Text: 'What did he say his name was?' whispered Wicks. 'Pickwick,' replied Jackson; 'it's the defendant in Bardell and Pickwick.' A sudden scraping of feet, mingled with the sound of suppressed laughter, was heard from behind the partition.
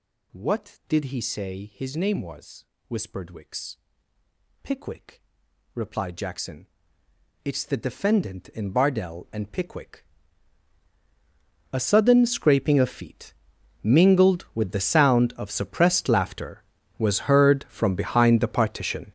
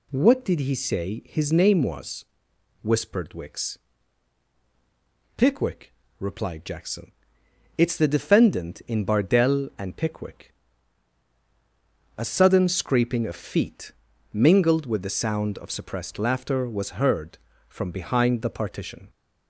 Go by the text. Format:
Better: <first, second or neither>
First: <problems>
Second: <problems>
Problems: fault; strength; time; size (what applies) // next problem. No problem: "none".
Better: second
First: gets louder; strong; throughout; 12.5 dB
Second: none